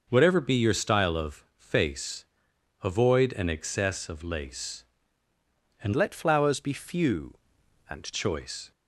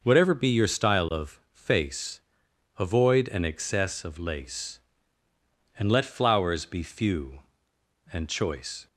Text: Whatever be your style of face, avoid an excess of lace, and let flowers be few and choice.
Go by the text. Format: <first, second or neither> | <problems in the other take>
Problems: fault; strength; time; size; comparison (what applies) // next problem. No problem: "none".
second | changes voice from "let" to "and"; from 5.9 to 8.1 s; 2.2 s long